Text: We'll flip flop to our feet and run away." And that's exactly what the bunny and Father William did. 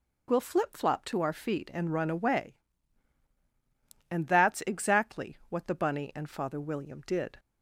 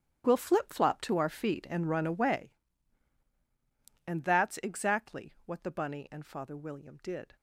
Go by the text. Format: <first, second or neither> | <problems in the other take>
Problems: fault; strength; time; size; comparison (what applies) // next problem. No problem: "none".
first | gets quieter; strong; throughout; 15 dB